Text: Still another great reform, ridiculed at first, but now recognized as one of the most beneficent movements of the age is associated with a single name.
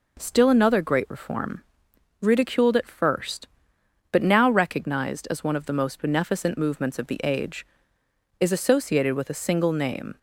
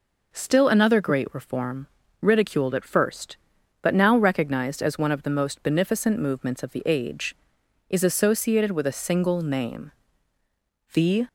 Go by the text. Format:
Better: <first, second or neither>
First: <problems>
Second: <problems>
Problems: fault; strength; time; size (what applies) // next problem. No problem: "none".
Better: first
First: none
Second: goes on to say "The"; slight; from 10.9 s on; 0.32 s long